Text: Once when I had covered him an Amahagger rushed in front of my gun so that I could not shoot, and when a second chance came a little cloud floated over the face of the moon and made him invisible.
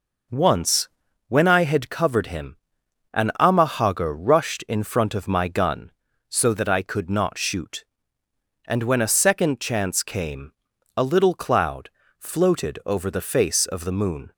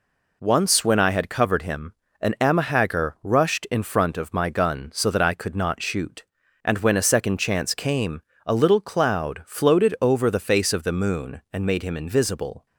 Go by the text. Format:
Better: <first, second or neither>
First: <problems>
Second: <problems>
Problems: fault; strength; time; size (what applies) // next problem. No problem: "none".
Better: second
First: pauses between "Once" and "when"; at 0.8 s; 0.40 s long // pauses between "him" and "an"; noticeable; at 2.5 s; 0.58 s long // pauses between "came" and "a"; noticeable; at 10.5 s; 0.46 s long // pauses between "cloud" and "floated"; slight; at 11.9 s; 0.28 s long // stops before "and made him invisible"; at 14.3 s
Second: pauses between "him" and "an"; slight; at 1.9 s; 0.26 s long // pauses between "came" and "a"; slight; at 8.2 s; 0.24 s long